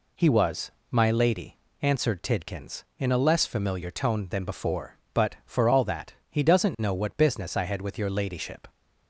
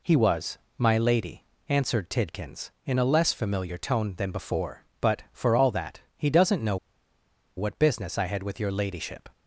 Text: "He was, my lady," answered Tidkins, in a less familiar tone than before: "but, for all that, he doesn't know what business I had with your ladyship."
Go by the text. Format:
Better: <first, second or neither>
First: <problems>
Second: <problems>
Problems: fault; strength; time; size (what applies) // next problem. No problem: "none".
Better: first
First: none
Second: pauses between "know" and "what"; noticeable; at 6.7 s; 0.80 s long